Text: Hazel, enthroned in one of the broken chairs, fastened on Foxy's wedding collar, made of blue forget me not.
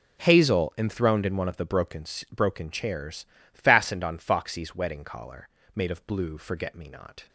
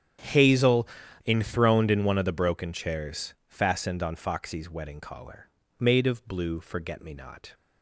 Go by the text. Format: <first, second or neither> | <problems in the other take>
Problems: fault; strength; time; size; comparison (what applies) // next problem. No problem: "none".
second | starts louder than the rest; strong; until 1.2 s; 9.5 dB; strong in the second // says "broken" twice; at 2.3 s